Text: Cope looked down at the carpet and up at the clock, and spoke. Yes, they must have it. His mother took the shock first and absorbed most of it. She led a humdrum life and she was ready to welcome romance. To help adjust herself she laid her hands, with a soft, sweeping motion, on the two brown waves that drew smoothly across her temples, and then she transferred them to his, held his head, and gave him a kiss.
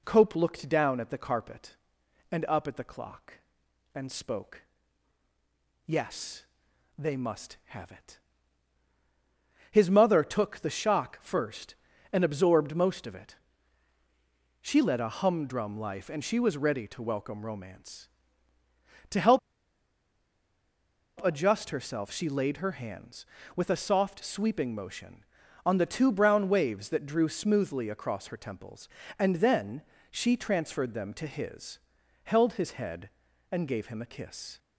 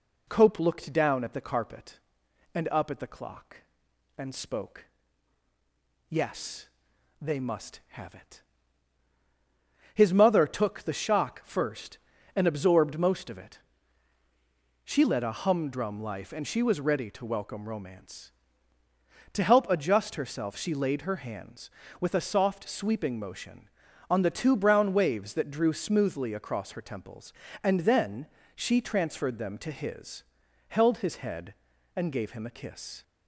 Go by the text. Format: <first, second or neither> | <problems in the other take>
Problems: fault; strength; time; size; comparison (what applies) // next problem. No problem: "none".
second | pauses between "help" and "adjust"; strong; at 19.3 s; 1.8 s long // pauses between "then" and "she"; slight; at 29.8 s; 0.28 s long; slight in the second